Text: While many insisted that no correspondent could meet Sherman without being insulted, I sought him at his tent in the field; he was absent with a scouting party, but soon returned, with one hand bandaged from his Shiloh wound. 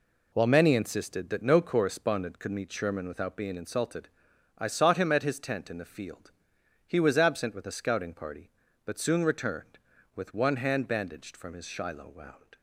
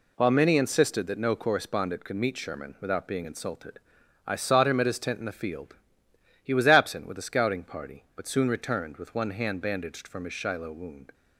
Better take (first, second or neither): neither